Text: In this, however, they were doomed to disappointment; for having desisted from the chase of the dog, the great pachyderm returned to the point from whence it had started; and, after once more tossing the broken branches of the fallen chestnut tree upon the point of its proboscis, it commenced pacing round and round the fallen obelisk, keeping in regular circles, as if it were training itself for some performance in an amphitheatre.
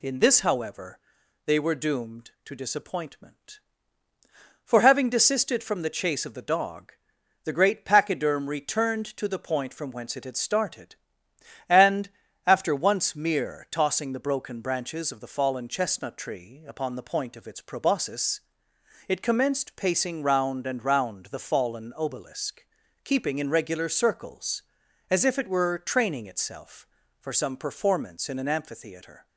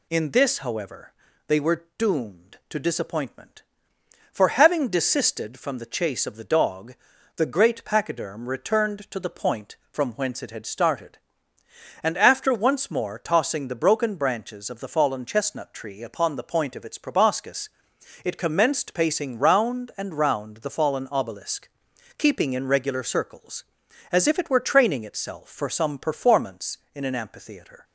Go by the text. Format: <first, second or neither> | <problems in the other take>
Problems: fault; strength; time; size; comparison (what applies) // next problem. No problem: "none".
second | says "mere" for "more"; at 13.1 s